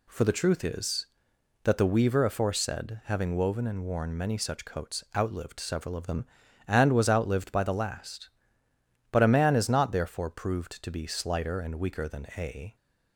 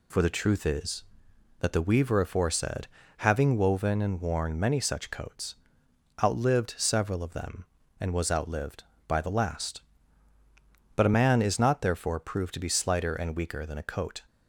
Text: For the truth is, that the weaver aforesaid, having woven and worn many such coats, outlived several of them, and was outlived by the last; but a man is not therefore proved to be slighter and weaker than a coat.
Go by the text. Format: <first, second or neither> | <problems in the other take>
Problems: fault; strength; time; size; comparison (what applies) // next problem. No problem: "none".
second | stops before "coat"; at 12.7 s